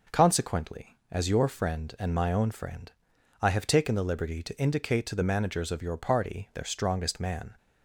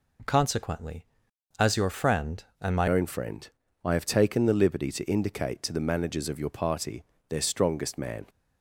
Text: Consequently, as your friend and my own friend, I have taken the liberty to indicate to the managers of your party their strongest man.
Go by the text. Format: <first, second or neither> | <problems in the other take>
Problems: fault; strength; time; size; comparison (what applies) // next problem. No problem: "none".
first | changes voice at "own"; from 2.8 s on; 5.4 s long // pauses between "party" and "their"; slight; at 7.0 s; 0.24 s long